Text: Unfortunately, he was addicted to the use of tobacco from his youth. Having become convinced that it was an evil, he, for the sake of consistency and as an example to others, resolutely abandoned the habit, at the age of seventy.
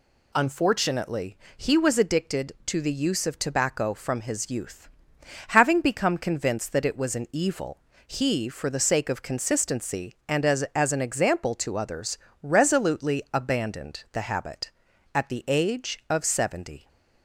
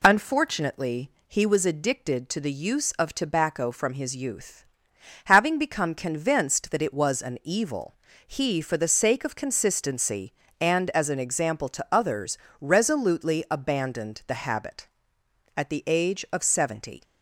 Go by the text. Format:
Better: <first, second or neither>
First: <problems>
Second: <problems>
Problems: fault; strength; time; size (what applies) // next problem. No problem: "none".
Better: second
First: says "as" twice; at 10.7 s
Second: none